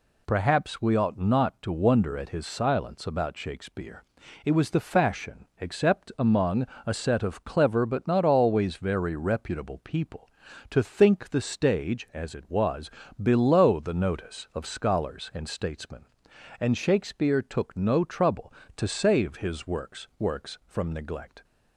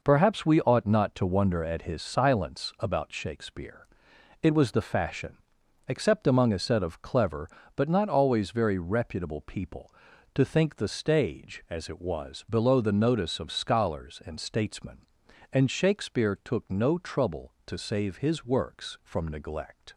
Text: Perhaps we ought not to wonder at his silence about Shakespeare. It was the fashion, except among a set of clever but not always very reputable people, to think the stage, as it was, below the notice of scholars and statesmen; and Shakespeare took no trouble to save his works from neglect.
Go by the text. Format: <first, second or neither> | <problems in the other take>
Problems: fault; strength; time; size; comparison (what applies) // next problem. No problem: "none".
second | pauses between "among" and "a"; slight; at 6.6 s; 0.22 s long // says "works" twice; at 20.1 s